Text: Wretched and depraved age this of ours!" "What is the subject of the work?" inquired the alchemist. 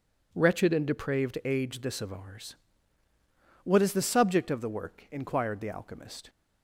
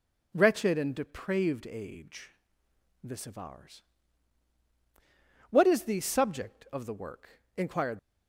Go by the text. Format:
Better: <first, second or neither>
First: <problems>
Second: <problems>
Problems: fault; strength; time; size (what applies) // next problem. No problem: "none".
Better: first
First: none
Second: pauses between "age" and "this"; noticeable; at 2.3 s; 0.72 s long // stops before "the alchemist"; at 7.9 s